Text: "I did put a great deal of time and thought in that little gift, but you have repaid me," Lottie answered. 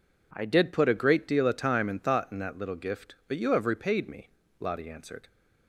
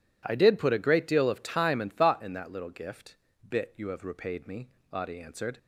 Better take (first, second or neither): first